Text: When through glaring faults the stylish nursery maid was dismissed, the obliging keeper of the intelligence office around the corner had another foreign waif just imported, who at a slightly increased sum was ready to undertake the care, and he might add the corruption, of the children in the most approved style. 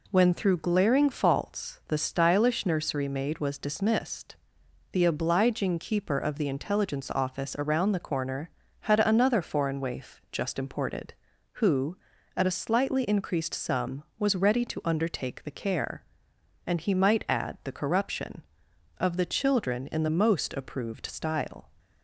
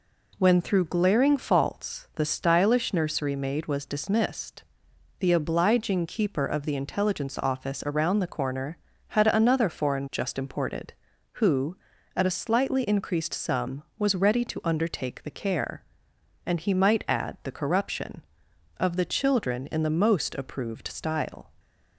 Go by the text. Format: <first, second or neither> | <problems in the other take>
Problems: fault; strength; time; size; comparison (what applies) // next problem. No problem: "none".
first | skips "waif"; at 10.0 s